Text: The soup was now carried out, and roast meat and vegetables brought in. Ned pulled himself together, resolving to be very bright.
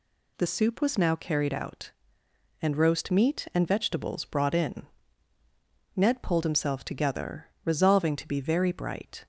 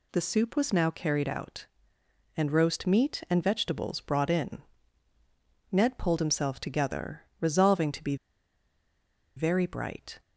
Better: first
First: none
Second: pauses between "be" and "very"; at 8.1 s; 1.2 s long

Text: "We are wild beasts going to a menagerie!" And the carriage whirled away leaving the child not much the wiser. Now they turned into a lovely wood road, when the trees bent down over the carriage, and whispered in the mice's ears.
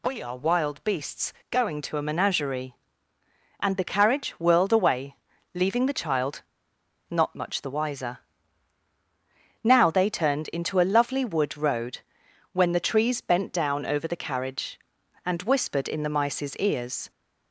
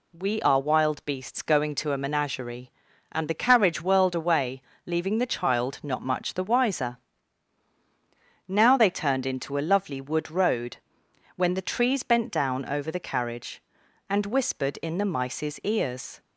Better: second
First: pauses between "beasts" and "going"; slight; at 1.3 s; 0.18 s long // pauses between "away" and "leaving"; at 5.1 s; 0.40 s long // pauses between "child" and "not"; noticeable; at 6.4 s; 0.68 s long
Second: pauses between "away" and "leaving"; slight; at 4.5 s; 0.24 s long

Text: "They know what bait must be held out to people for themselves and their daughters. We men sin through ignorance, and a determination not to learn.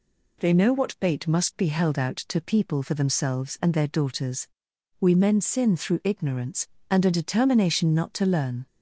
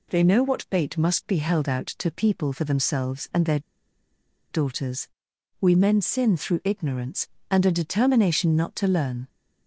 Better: first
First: none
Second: pauses between "their" and "daughters"; noticeable; at 3.5 s; 0.91 s long

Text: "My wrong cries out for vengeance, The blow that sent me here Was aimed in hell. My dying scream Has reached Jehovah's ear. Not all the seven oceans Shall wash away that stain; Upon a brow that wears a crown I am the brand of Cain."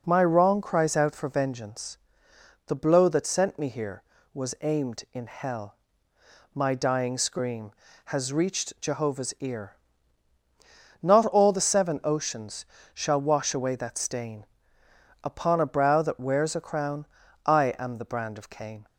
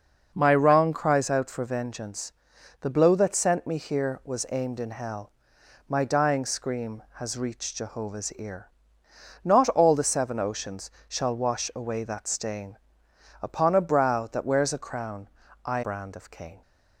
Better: first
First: pauses between "oceans" and "Shall"; slight; at 12.6 s; 0.28 s long // pauses between "crown" and "I"; at 17.0 s; 0.40 s long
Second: pauses between "oceans" and "Shall"; slight; at 10.8 s; 0.18 s long // pauses between "crown" and "I"; slight; at 15.2 s; 0.36 s long // skips "am the"; at 15.8 s

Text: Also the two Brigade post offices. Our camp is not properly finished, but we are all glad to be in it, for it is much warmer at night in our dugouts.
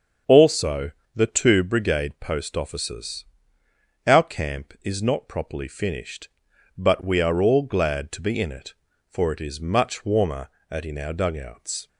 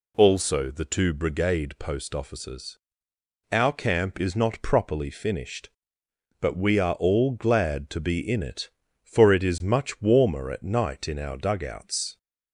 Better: second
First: starts louder than the rest; strong; until 1.5 s; 7 dB // pauses between "Also" and "the"; slight; at 0.9 s; 0.24 s long // skips "night"; at 10.8 s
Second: none

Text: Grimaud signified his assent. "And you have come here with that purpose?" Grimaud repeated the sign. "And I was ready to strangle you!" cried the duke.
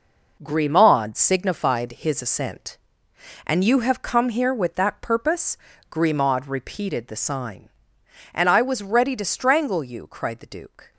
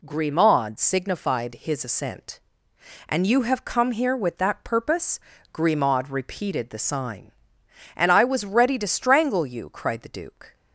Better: second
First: gets quieter; strong; throughout; 8.5 dB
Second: none

